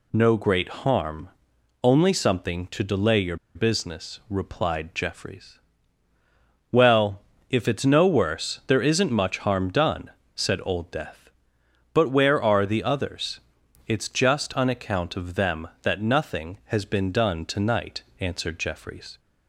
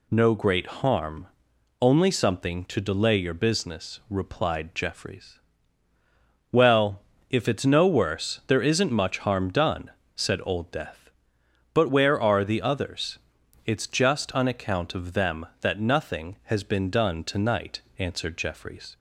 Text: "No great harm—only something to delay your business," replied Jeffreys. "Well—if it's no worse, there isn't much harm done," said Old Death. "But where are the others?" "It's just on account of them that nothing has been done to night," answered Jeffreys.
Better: second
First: pauses between "your" and "business"; slight; at 3.3 s; 0.19 s long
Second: none

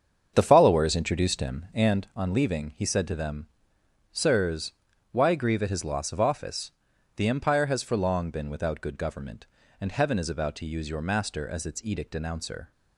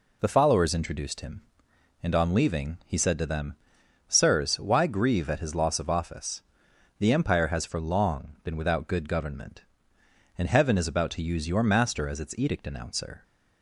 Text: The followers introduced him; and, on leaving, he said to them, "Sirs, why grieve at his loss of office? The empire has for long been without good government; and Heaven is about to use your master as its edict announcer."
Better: second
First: starts louder than the rest; strong; until 2.1 s; 7.5 dB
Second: none

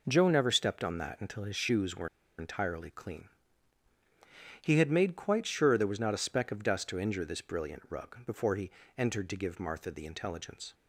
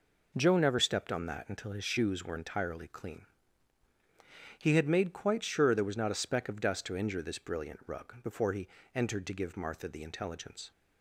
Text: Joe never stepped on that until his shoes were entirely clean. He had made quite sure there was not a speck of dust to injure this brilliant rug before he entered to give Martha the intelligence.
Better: second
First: pauses between "were" and "entirely"; slight; at 2.0 s; 0.30 s long // pauses between "he" and "entered"; slight; at 8.6 s; 0.26 s long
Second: pauses between "he" and "entered"; slight; at 8.6 s; 0.26 s long

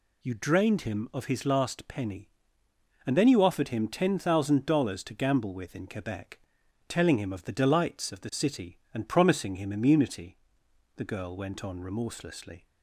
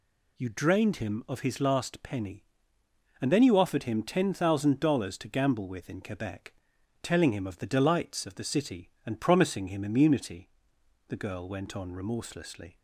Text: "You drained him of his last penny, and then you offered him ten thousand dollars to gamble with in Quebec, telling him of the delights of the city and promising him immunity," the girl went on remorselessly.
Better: neither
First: none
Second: none

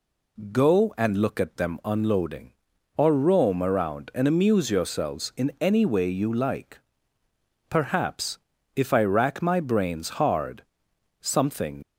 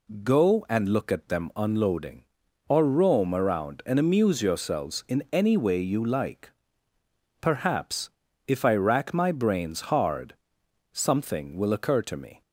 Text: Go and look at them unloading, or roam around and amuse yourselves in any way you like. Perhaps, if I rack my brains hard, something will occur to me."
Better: second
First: stops before "will occur to me"; at 11.8 s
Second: none

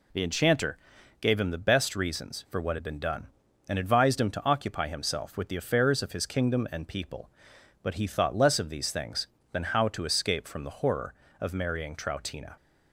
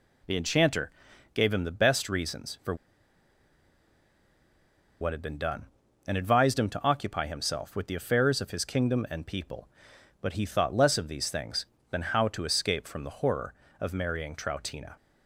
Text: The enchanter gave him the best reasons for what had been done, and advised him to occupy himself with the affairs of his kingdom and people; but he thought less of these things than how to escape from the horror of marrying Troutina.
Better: first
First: pauses between "enchanter" and "gave"; at 0.7 s; 0.44 s long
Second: pauses between "enchanter" and "gave"; at 0.9 s; 0.44 s long // pauses between "for" and "what"; strong; at 2.7 s; 2.2 s long

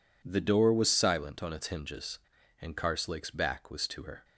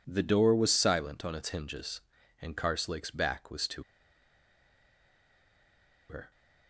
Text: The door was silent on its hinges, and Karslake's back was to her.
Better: first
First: none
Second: pauses between "to" and "her"; strong; at 3.8 s; 2.2 s long

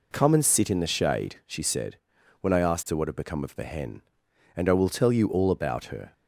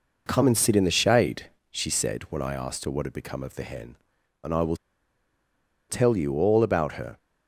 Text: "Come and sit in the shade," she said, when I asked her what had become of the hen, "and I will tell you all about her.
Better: first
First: none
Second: pauses between "will" and "tell"; at 4.7 s; 1.1 s long

